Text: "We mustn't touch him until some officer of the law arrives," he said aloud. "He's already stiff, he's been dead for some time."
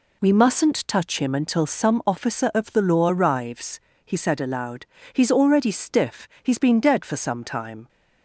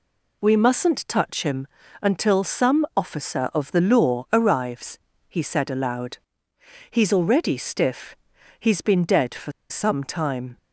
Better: first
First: none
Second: pauses between "him" and "until"; slight; at 1.6 s; 0.34 s long // pauses between "for" and "some"; slight; at 9.5 s; 0.19 s long

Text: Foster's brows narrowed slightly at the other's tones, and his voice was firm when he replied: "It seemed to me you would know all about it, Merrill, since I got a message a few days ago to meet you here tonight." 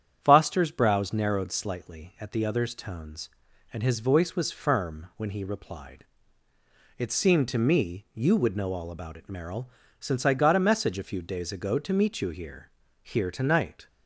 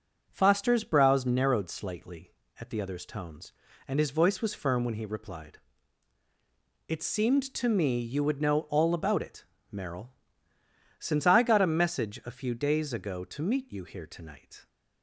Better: second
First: starts louder than the rest; strong; until 1.2 s; 9 dB // says "here" twice; at 13.0 s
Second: none

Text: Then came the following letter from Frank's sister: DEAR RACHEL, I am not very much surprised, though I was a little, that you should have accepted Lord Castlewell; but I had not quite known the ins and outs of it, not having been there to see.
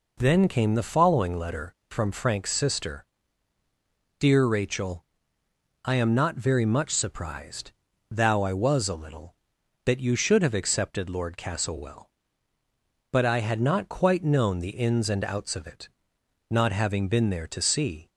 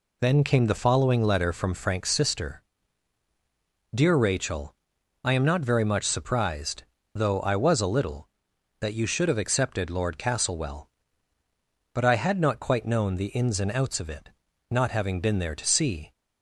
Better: second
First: says "thou" for "though"; at 8.1 s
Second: none

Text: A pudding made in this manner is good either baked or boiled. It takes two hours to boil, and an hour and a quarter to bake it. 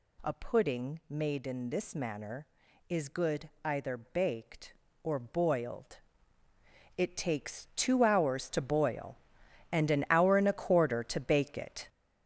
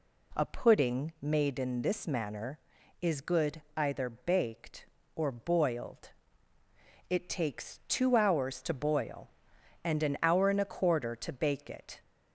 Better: second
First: gets louder; strong; throughout; 7.5 dB // pauses between "good" and "either"; slight; at 3.4 s; 0.16 s long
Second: pauses between "good" and "either"; slight; at 3.5 s; 0.16 s long

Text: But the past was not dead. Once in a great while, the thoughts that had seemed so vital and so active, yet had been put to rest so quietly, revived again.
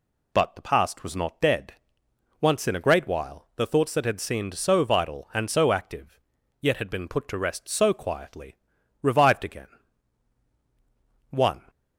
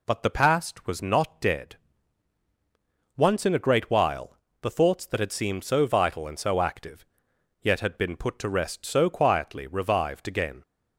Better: second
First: goes on to say "One"; slight; from 11.2 s on; 0.40 s long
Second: none

